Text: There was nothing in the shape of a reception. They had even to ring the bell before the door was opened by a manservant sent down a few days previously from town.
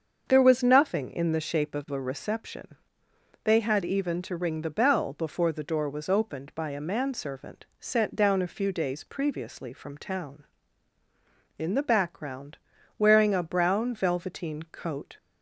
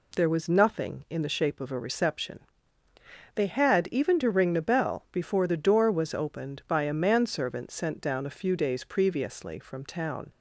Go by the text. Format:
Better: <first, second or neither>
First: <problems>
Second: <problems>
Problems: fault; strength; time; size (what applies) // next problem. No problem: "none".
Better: second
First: starts louder than the rest; until 1.3 s; 7 dB // pauses between "manservant" and "sent"; slight; at 7.6 s; 0.16 s long // goes on to say "In the background wearing a brown velveteen coat"; strong; from 11.5 s on; 3.5 s long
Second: none